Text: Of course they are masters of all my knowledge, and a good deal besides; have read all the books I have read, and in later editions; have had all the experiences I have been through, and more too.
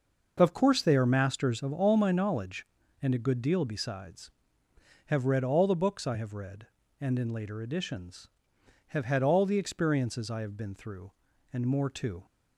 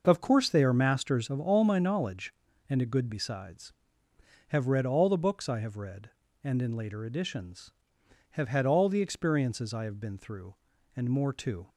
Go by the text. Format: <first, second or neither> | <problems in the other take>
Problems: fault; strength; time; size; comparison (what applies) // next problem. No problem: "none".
first | skips "deal"; at 3.0 s